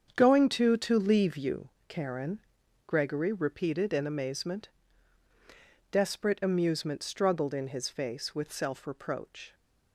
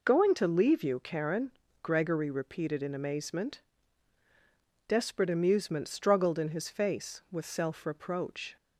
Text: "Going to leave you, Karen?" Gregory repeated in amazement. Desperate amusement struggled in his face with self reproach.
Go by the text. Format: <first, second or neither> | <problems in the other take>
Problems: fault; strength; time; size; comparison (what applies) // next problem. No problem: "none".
second | starts louder than the rest; strong; until 1.1 s; 7.5 dB // says "to" twice; at 0.7 s